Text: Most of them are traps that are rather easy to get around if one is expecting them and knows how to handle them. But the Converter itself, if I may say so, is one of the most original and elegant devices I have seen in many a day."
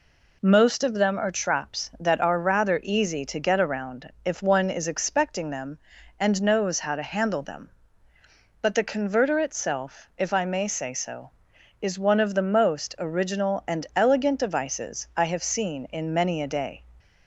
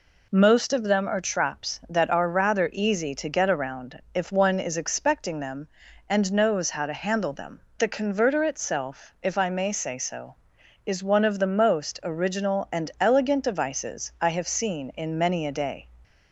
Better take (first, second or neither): first